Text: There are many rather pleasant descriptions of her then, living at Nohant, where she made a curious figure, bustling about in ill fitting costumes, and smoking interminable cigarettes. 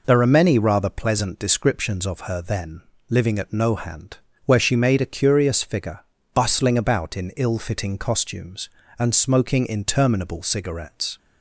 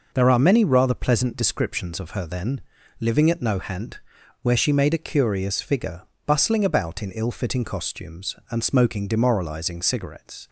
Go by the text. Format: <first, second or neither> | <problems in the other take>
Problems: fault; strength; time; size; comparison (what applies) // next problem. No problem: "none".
first | says "demoralizing" for "interminable"; at 9.0 s